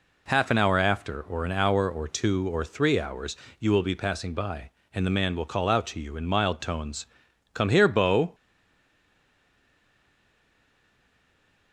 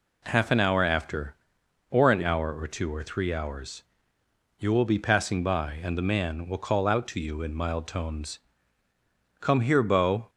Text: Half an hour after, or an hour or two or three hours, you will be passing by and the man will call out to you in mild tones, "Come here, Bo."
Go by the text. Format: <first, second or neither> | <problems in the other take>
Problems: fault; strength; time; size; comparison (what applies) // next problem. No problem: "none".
second | stays silent after the last word; strong; from 8.3 s on; 3.4 s long